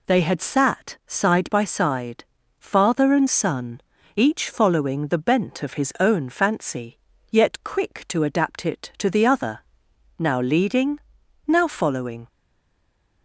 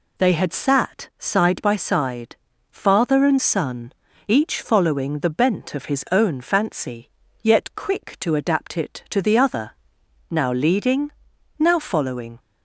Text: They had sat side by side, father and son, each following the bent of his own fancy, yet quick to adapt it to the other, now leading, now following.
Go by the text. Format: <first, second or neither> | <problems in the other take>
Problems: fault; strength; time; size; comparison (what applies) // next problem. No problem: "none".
second | stays silent after the last word; from 12.2 s on; 1.0 s long